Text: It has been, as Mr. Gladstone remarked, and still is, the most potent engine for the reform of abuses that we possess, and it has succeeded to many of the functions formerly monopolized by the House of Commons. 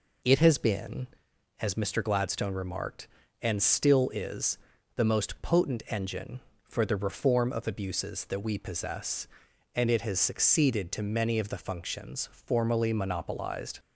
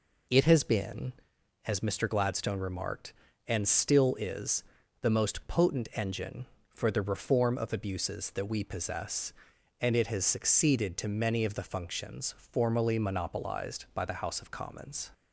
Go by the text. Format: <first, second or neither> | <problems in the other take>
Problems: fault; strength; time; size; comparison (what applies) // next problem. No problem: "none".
second | stops before "by the House of Commons"; at 13.7 s